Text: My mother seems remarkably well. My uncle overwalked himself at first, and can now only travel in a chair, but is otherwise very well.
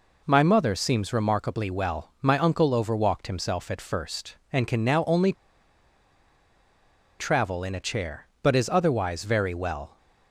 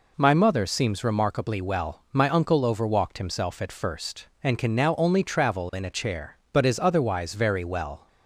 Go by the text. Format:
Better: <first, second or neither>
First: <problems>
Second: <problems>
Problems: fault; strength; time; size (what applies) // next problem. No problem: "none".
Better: second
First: pauses between "only" and "travel"; strong; at 5.3 s; 1.8 s long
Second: none